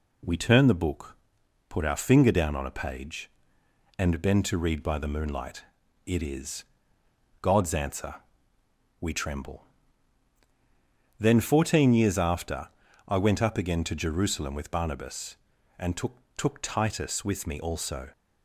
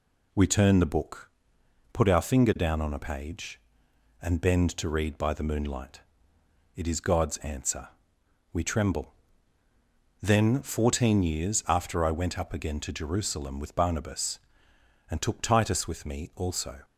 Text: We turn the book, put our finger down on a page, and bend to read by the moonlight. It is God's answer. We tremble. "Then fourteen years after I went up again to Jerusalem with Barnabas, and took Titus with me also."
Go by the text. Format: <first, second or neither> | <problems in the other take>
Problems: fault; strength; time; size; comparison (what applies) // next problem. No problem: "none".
second | pauses between "is" and "God's"; noticeable; at 6.6 s; 0.78 s long // pauses between "after" and "I"; at 12.6 s; 0.40 s long // says "took" twice; at 16.3 s